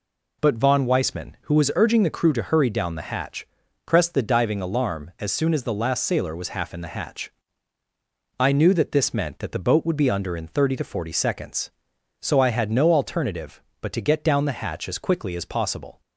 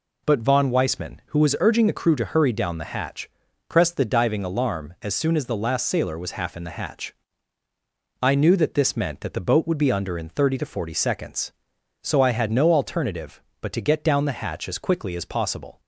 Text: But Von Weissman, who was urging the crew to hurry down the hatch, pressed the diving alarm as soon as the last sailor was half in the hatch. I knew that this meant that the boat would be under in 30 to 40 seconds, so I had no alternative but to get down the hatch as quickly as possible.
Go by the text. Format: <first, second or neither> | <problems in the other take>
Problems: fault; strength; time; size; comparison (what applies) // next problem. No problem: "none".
neither | none